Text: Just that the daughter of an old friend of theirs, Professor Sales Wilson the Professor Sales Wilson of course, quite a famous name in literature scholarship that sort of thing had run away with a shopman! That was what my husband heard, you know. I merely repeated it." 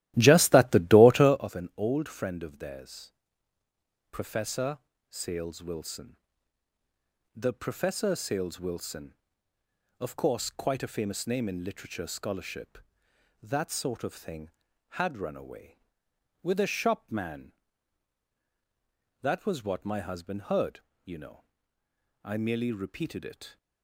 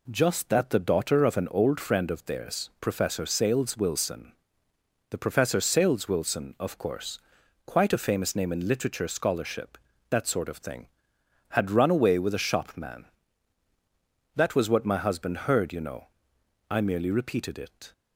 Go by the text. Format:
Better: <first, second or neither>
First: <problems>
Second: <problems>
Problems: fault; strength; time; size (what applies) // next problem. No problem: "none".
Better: second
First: starts louder than the rest; strong; until 1.5 s; 14.5 dB // pauses between "Professor" and "Sales"; slight; at 4.7 s; 0.30 s long // pauses between "Wilson" and "the"; at 6.1 s; 1.2 s long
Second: pauses between "Wilson" and "the"; noticeable; at 4.3 s; 0.78 s long